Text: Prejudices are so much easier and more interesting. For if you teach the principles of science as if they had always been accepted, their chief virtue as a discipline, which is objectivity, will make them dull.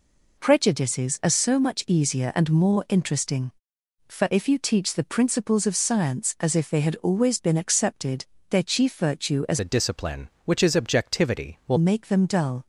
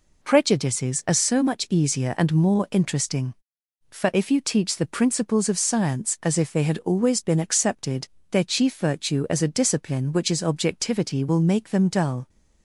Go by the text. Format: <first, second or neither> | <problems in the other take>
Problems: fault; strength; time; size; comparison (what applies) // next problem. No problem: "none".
second | changes voice from "a" to "will"; from 9.5 to 11.7 s; 2.2 s long